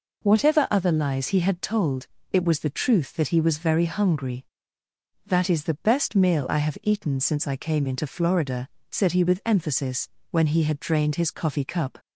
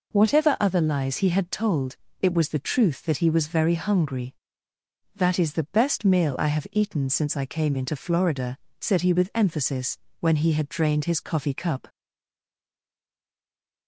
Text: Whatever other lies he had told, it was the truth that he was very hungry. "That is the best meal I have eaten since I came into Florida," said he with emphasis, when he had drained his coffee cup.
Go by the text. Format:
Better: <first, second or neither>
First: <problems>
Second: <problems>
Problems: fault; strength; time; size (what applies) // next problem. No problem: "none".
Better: first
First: none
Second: stays silent after the last word; noticeable; from 11.8 s on; 2.0 s long